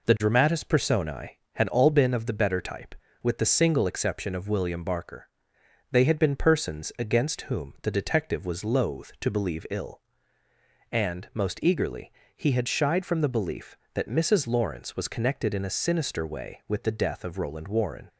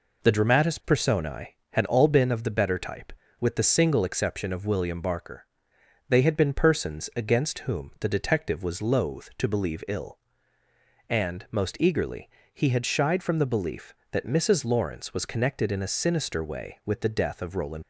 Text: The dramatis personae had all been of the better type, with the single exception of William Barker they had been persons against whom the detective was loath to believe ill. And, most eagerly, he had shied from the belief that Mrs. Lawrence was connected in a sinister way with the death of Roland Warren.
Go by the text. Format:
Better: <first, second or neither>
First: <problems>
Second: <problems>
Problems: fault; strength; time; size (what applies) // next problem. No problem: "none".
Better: first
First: pauses between "Barker" and "they"; noticeable; at 5.2 s; 0.62 s long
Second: pauses between "Barker" and "they"; noticeable; at 5.4 s; 0.62 s long // stops before "Warren"; at 17.8 s